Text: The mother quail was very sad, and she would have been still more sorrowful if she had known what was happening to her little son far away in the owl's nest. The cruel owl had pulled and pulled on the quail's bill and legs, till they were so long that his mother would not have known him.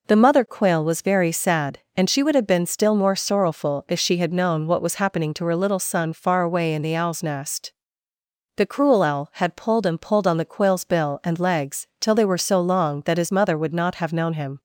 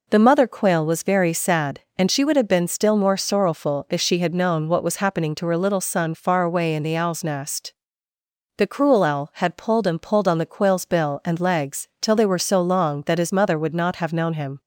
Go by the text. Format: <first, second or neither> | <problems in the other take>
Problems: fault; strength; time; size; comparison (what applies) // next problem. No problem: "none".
neither | none